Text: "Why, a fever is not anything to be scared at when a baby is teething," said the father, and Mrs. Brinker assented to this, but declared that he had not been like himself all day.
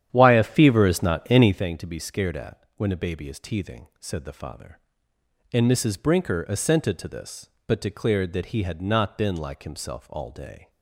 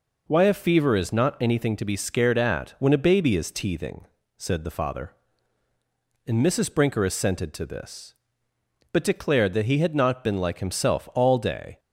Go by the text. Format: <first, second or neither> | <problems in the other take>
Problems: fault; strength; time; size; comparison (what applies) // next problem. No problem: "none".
second | starts louder than the rest; strong; until 1.6 s; 10 dB